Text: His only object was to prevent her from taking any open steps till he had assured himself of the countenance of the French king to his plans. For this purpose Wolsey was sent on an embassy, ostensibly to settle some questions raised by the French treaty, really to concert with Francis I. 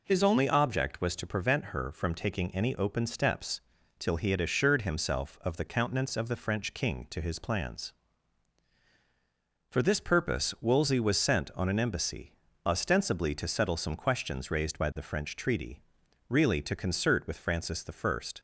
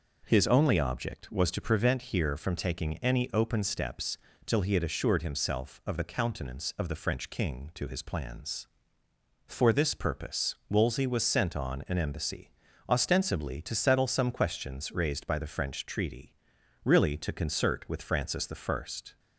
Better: first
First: pauses between "steps" and "till"; at 3.5 s; 0.38 s long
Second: says "here" for "her"; at 2.0 s // pauses between "steps" and "till"; slight; at 4.1 s; 0.30 s long

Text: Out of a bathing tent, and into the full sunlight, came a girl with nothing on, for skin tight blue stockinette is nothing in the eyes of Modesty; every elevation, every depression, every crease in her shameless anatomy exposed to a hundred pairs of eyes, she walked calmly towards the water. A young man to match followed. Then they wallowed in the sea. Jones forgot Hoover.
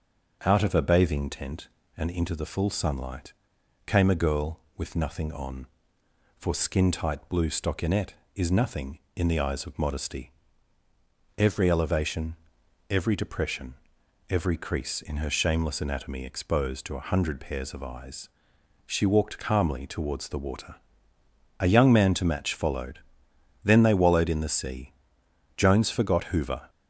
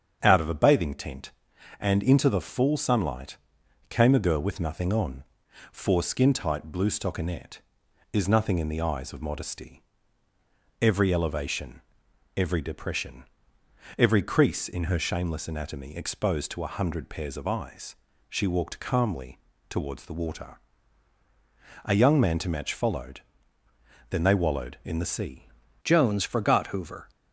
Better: first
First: starts louder than the rest; until 1.4 s; 6.5 dB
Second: starts louder than the rest; strong; until 1.2 s; 7.5 dB // pauses between "calmly" and "towards"; slight; at 19.3 s; 0.32 s long // changes voice at "Jones"; from 25.8 s on; 1.2 s long

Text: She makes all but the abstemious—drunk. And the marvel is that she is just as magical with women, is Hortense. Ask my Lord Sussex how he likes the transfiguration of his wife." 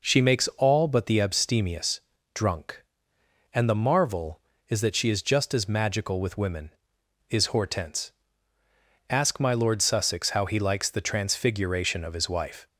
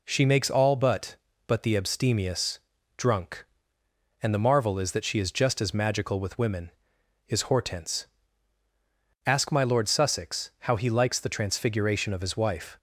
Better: first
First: none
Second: says "but" twice; at 1.4 s

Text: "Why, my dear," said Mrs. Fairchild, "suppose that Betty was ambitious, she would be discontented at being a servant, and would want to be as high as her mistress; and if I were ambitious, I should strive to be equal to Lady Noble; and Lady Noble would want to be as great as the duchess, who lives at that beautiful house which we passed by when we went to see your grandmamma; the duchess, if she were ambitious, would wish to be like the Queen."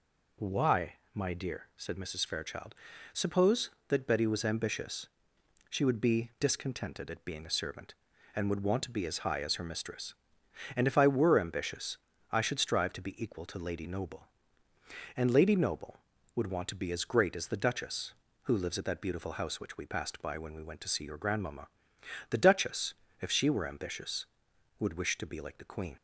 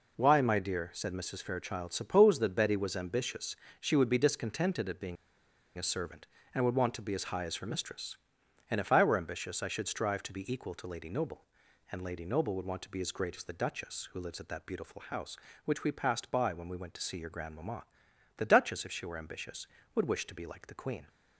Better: first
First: none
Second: pauses between "being" and "a"; noticeable; at 5.1 s; 0.62 s long

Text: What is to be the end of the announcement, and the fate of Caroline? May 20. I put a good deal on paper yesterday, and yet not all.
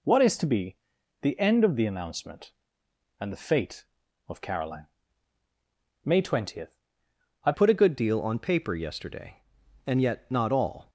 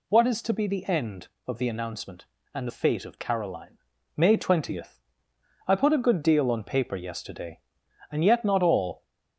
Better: second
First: pauses between "be" and "the"; at 0.7 s; 0.44 s long // changes voice at "put"; from 7.5 s on; 3.3 s long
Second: none

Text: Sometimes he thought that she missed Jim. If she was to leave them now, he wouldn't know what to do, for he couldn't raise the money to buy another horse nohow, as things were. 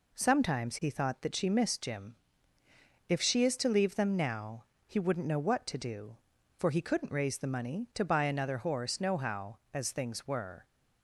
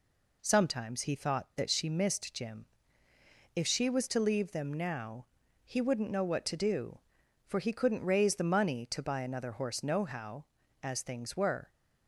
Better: second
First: says "is" for "was"; at 3.4 s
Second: none

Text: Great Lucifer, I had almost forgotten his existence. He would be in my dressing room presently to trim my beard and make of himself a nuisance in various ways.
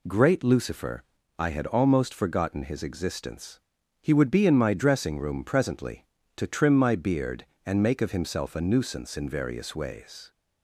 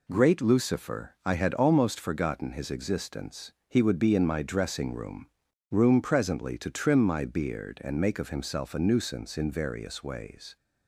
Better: first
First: none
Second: says "room" twice; at 5.7 s

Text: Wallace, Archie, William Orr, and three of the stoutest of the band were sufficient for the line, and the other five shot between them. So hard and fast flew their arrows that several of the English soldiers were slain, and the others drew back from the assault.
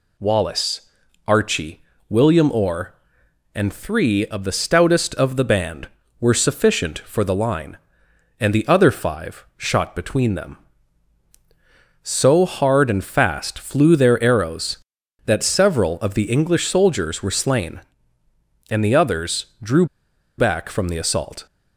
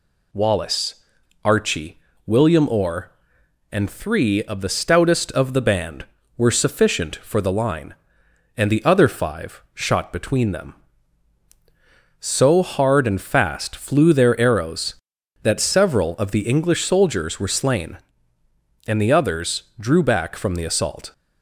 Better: second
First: pauses between "drew" and "back"; noticeable; at 19.8 s; 0.52 s long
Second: none

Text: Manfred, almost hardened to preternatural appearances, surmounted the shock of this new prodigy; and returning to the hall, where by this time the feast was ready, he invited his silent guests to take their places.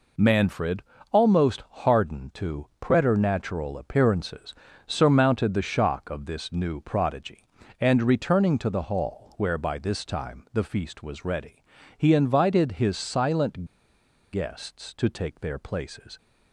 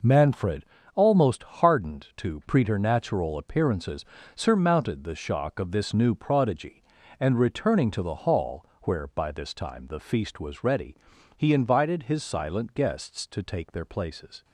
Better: second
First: pauses between "silent" and "guests"; noticeable; at 13.6 s; 0.66 s long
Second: none

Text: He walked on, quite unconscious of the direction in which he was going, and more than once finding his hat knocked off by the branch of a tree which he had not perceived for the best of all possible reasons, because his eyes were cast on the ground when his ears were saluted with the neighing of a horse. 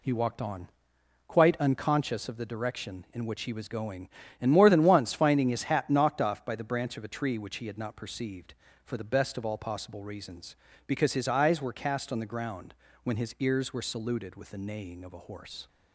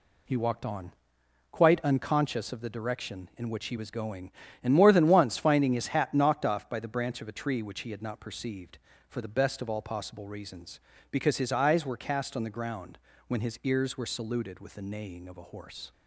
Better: neither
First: pauses between "ground" and "when"; slight; at 12.7 s; 0.30 s long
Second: pauses between "ground" and "when"; slight; at 12.9 s; 0.30 s long

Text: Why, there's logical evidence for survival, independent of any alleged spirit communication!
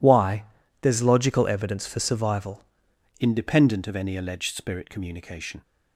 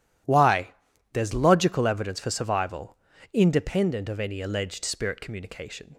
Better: second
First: changes voice at "independent"; from 3.2 s on; 2.4 s long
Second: none

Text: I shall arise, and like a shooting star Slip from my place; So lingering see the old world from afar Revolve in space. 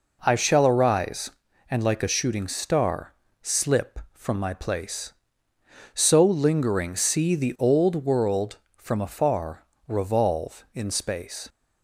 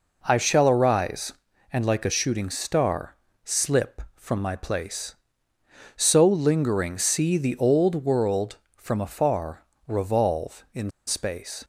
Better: first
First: pauses between "star" and "Slip"; slight; at 3.1 s; 0.28 s long // pauses between "afar" and "Revolve"; slight; at 9.6 s; 0.24 s long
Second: pauses between "star" and "Slip"; slight; at 3.1 s; 0.28 s long // pauses between "afar" and "Revolve"; slight; at 9.6 s; 0.24 s long // pauses between "in" and "space"; slight; at 10.9 s; 0.17 s long

